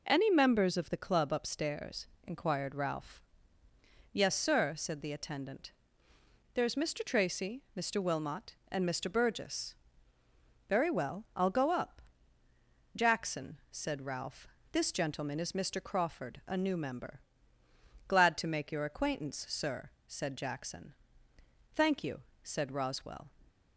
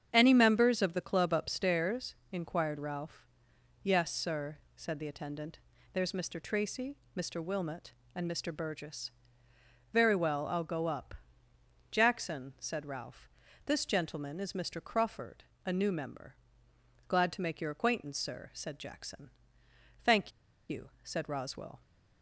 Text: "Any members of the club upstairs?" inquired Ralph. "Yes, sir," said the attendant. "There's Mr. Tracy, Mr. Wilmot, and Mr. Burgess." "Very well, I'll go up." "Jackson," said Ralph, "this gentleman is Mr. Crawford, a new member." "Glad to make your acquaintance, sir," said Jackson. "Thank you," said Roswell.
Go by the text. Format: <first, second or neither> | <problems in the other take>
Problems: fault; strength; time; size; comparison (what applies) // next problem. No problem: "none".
first | starts louder than the rest; strong; until 1.1 s; 8 dB // pauses between "Thank" and "you"; at 20.3 s; 0.38 s long